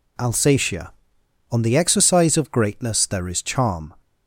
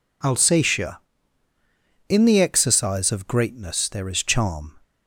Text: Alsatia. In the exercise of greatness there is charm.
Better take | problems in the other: second | says "On" for "In"; at 1.5 s

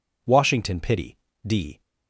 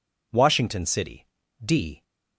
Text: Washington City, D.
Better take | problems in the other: second | says "Pity" for "City"; at 0.8 s

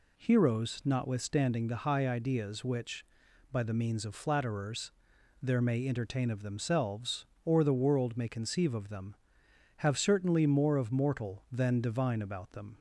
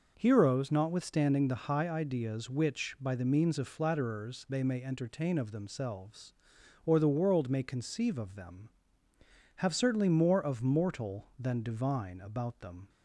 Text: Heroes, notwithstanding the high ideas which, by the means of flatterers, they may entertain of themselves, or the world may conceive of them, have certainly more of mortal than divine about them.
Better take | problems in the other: second | says "there" for "they"; at 5.4 s

